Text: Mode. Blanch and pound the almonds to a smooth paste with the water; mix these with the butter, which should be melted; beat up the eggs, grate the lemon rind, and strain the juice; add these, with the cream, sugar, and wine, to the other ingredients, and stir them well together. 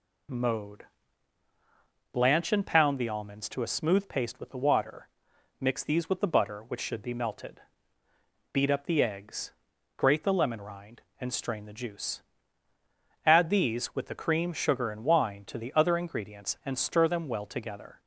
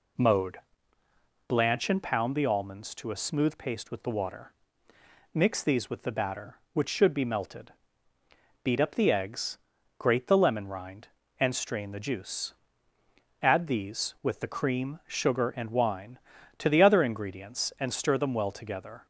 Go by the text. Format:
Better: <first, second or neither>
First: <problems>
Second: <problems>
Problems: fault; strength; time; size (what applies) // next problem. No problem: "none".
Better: first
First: none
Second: says "batter" for "butter"; at 6.1 s